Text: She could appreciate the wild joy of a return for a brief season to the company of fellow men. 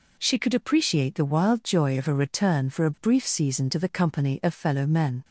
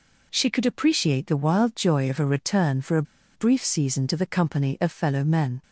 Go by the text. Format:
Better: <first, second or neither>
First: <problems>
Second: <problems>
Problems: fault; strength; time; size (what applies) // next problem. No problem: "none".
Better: first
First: none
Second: pauses between "a" and "brief"; slight; at 3.0 s; 0.31 s long